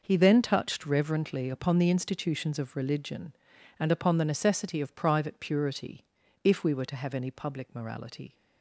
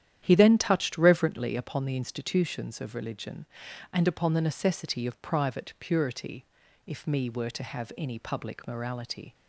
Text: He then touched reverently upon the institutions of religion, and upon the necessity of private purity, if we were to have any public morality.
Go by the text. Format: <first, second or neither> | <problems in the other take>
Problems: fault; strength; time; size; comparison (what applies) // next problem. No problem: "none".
first | starts louder than the rest; strong; until 1.2 s; 10.5 dB // says "me" for "we"; at 7.0 s